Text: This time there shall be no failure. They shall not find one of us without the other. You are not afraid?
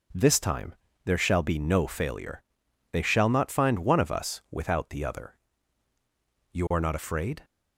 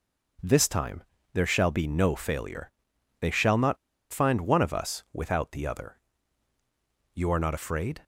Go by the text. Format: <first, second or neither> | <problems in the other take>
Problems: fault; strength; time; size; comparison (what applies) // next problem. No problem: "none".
first | pauses between "time" and "there"; slight; at 1.0 s; 0.32 s long; slight in the first // pauses between "not" and "find"; at 3.7 s; 0.36 s long